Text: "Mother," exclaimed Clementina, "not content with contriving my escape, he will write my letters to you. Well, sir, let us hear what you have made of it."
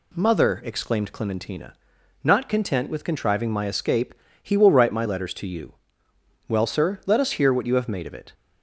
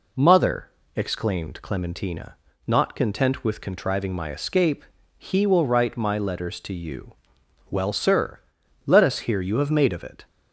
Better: first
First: none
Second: skips "what"; at 9.4 s

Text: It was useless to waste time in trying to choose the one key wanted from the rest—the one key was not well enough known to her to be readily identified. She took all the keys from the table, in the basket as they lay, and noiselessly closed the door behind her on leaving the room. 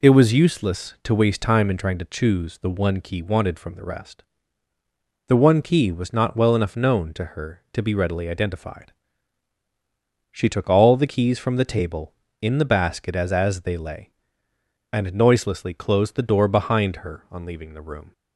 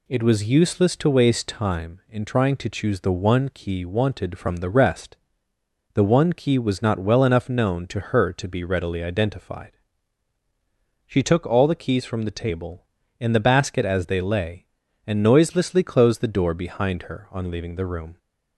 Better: second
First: says "as" twice; at 13.3 s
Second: none

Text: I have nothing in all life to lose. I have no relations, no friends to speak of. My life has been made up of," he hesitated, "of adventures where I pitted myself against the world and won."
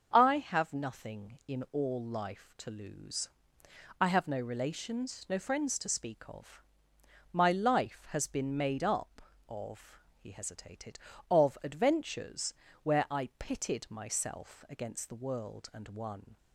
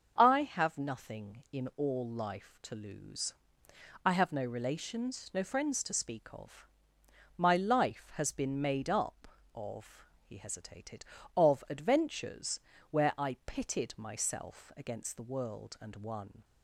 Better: neither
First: starts louder than the rest; until 1.1 s; 6.5 dB // pauses between "adventures" and "where"; slight; at 12.5 s; 0.26 s long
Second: starts louder than the rest; until 1.1 s; 6.5 dB // pauses between "adventures" and "where"; slight; at 12.6 s; 0.28 s long

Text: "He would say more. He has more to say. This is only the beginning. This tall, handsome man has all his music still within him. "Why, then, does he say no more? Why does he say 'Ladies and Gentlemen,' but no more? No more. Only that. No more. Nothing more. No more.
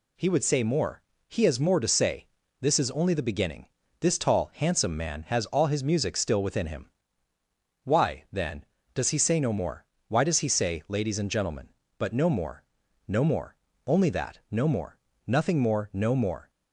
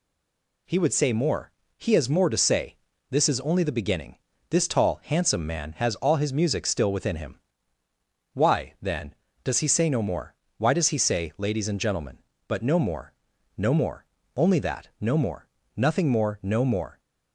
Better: first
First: none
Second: stays silent before the first word; slight; until 0.6 s; 0.6 s long

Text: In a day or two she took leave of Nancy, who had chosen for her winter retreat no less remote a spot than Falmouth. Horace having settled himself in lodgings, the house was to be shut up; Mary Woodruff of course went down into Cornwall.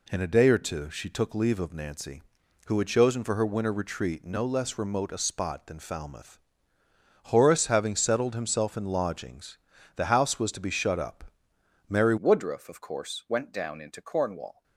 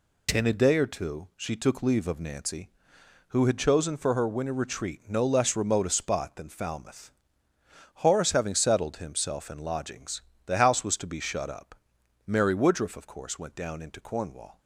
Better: second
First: changes voice at "Woodruff"; from 12.1 s on; 2.5 s long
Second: none

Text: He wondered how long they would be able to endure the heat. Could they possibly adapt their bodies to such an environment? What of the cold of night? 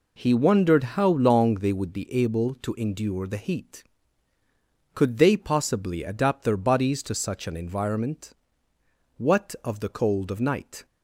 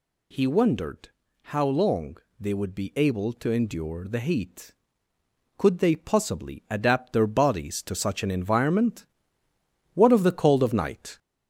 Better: first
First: none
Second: gets louder; slight; throughout; 2.5 dB // pauses between "wondered" and "how"; at 1.0 s; 0.42 s long // pauses between "long" and "they"; slight; at 2.1 s; 0.24 s long

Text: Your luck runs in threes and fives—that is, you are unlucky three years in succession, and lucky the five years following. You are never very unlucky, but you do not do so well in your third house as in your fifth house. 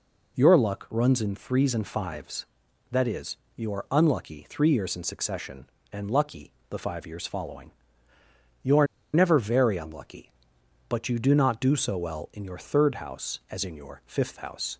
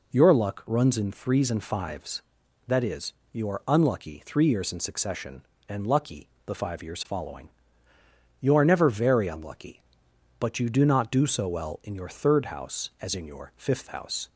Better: second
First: pauses between "lucky" and "the"; slight; at 6.5 s; 0.20 s long // pauses between "are" and "never"; slight; at 8.8 s; 0.27 s long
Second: pauses between "lucky" and "the"; slight; at 6.2 s; 0.20 s long

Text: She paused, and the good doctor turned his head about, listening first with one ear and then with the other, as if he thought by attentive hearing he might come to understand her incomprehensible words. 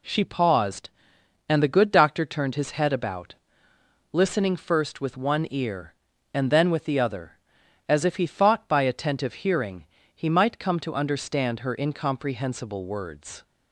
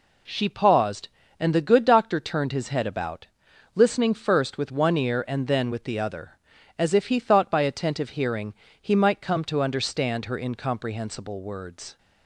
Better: neither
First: pauses between "hearing" and "he"; slight; at 9.8 s; 0.30 s long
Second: pauses between "hearing" and "he"; slight; at 8.5 s; 0.28 s long

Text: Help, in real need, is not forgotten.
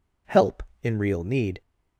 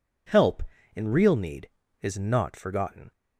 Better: second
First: stops before "is not forgotten"; at 1.6 s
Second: none

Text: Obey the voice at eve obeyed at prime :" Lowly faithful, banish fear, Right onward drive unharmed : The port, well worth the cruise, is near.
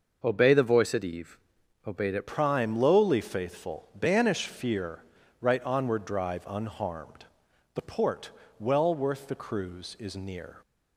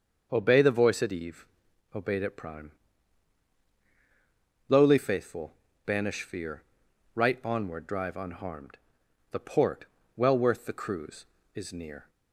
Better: second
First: pauses between "eve" and "obeyed"; noticeable; at 1.3 s; 0.48 s long // changes voice at "prime"; from 2.2 s on; 8.3 s long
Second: pauses between "eve" and "obeyed"; noticeable; at 1.4 s; 0.48 s long

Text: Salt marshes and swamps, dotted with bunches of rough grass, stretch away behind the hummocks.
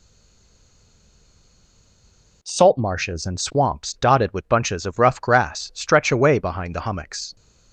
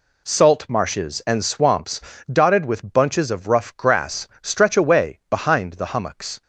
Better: second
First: stays silent before the first word; until 2.4 s; 2.4 s long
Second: none

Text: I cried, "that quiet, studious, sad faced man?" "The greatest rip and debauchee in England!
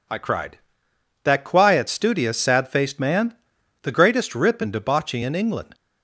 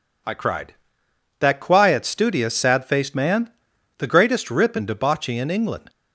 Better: neither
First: none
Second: none

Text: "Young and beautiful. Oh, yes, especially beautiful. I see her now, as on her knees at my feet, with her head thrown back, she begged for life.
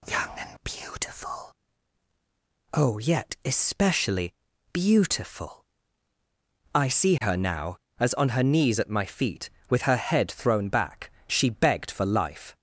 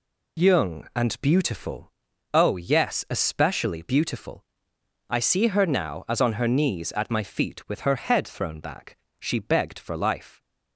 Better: second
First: says "yet" for "yes"; at 2.9 s // pauses between "especially" and "beautiful"; at 4.3 s; 0.38 s long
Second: none

